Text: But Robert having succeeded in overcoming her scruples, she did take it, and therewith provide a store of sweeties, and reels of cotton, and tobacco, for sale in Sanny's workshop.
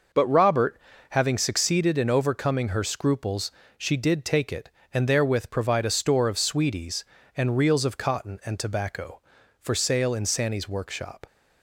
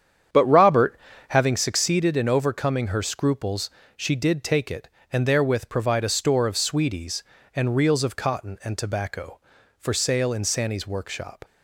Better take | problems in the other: first | starts louder than the rest; strong; until 1.6 s; 8.5 dB // pauses between "Robert" and "having"; slight; at 0.9 s; 0.32 s long; slight in the first

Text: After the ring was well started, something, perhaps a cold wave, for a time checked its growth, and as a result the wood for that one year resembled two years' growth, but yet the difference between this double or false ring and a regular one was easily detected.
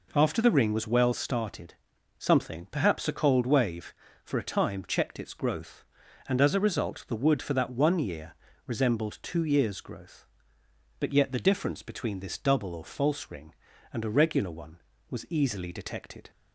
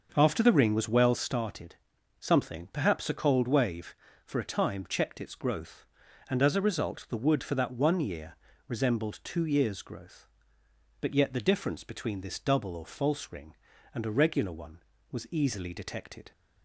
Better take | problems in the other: first | starts louder than the rest; until 1.4 s; 6.5 dB // pauses between "year" and "resembled"; slight; at 8.3 s; 0.32 s long; slight in the first

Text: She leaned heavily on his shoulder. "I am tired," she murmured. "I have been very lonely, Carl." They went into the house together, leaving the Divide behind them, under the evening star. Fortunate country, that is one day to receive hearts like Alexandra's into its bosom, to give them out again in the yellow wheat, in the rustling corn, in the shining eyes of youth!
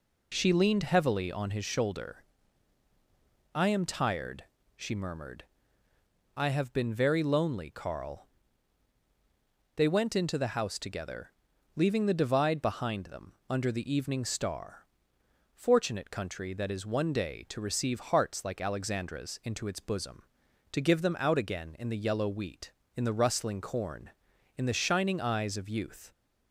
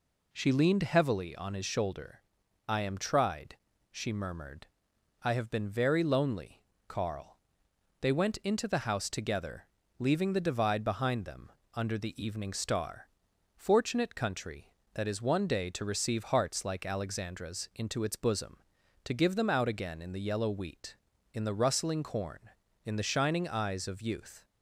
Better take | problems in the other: first | says "tried" for "tired"; at 2.9 s

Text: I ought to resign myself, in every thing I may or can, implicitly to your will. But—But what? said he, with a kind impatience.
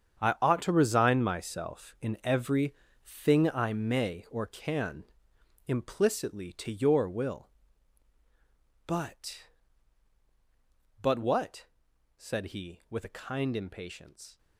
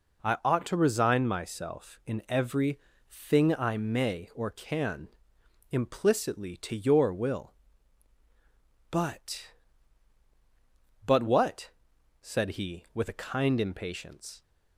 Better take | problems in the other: second | gets quieter; strong; throughout; 13 dB // pauses between "every" and "thing"; slight; at 2.7 s; 0.30 s long; slight in the second

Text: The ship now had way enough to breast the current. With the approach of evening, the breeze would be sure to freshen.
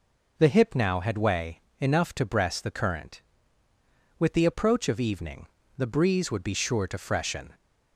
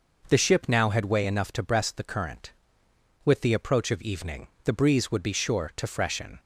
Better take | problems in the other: second | says "hip" for "ship"; at 0.4 s // pauses between "way" and "enough"; slight; at 1.6 s; 0.18 s long

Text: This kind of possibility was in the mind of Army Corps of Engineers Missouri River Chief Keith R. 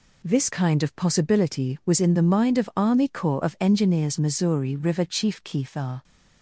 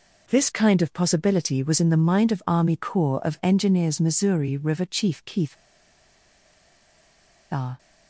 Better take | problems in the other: first | pauses between "Keith" and "R"; strong; at 5.5 s; 1.9 s long

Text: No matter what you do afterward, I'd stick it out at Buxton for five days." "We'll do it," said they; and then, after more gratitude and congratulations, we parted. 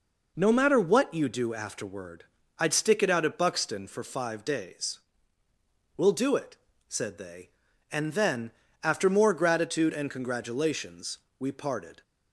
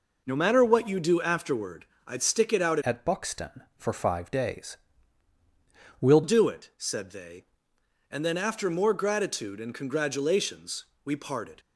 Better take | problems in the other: first | changes voice from "at" to "We'll"; from 2.8 to 6.2 s; 3.4 s long

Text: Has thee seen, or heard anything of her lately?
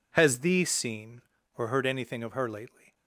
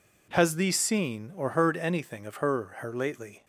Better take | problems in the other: first | says "her" twice; at 2.8 s

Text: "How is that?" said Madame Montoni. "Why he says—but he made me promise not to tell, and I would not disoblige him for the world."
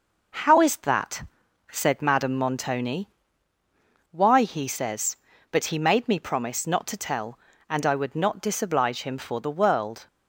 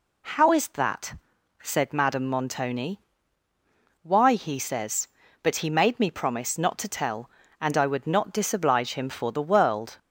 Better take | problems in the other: second | gets quieter; noticeable; throughout; 5.5 dB

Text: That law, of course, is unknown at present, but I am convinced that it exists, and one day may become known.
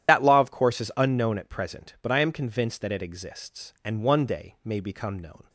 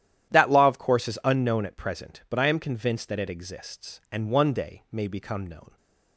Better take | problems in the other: second | loses the start of "That"; at 0.0 s; 60 ms // starts louder than the rest; strong; until 1.1 s; 11 dB; strong in the second

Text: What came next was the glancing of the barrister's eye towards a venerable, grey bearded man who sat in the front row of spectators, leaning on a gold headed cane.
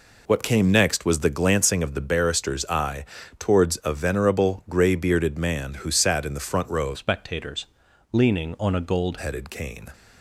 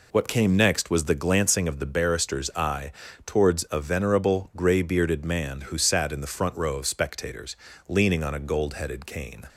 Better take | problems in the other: second | pauses between "eye" and "towards"; slight; at 3.0 s; 0.34 s long; slight in the second // changes voice from "spectators" to "gold"; from 6.9 to 9.1 s; 2.2 s long

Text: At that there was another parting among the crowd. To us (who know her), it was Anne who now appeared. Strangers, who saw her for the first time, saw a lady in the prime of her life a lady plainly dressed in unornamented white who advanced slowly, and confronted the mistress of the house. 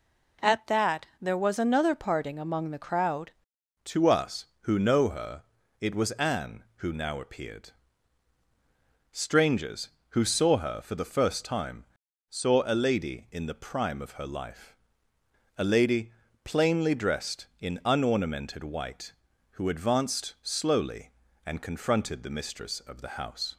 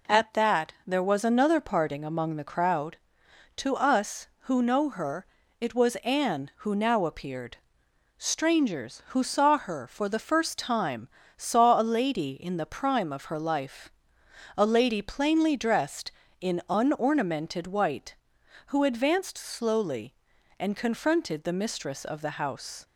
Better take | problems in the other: second | changes voice at "To"; from 3.8 s on; 19.7 s long // pauses between "life" and "a"; noticeable; at 14.7 s; 0.86 s long; noticeable in the second // pauses between "lady" and "plainly"; slight; at 16.1 s; 0.32 s long

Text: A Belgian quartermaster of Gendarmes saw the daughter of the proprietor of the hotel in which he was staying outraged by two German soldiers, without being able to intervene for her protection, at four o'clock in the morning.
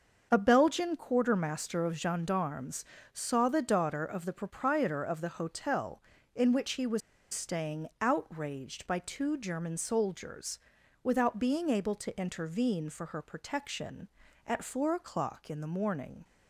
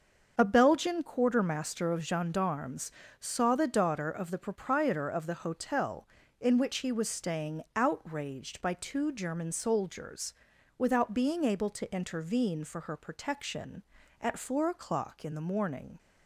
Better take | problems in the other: second | starts louder than the rest; until 1.3 s; 6.5 dB; also in the second // pauses between "Gendarmes" and "saw"; slight; at 2.8 s; 0.30 s long; slight in the second // pauses between "was" and "staying"; slight; at 7.0 s; 0.33 s long

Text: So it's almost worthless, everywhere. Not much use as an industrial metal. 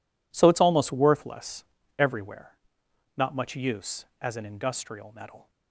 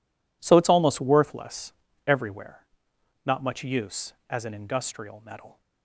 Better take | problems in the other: neither | none

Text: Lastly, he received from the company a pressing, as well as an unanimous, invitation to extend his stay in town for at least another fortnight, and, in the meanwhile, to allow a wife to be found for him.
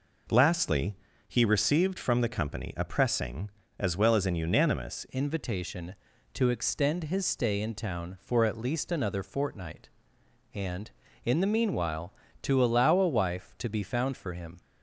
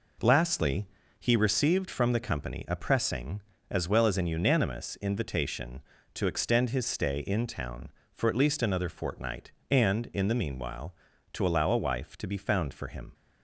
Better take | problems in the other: second | changes voice at "invitation"; from 5.1 s on; 9.5 s long

